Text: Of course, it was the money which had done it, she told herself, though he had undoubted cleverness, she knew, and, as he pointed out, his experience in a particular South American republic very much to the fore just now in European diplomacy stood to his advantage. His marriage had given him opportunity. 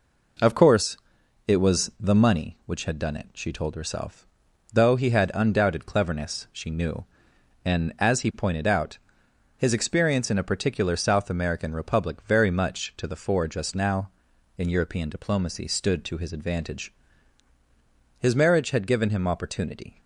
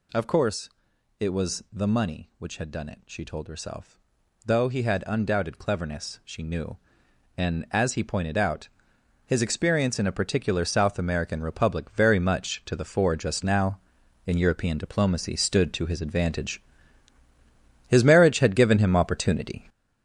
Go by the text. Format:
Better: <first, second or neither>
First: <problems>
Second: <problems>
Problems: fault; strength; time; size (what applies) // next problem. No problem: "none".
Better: first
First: none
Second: gets louder; throughout; 7 dB